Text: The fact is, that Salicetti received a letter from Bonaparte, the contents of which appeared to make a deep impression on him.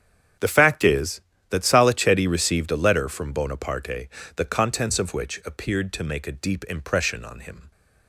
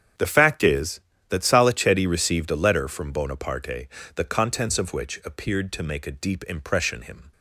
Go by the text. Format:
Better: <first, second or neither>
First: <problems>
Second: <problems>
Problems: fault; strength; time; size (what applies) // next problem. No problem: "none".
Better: first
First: starts louder than the rest; strong; until 1.6 s; 8.5 dB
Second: starts louder than the rest; strong; until 1.4 s; 8.5 dB // skips "on"; at 7.0 s